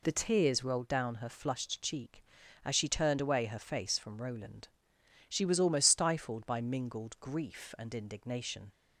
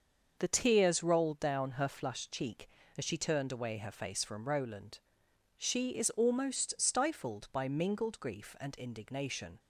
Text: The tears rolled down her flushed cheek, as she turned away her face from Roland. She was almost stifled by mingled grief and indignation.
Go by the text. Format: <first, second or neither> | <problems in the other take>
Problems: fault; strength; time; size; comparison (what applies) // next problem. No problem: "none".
first | starts louder than the rest; until 1.4 s; 6.5 dB // says "is" for "was"; at 5.9 s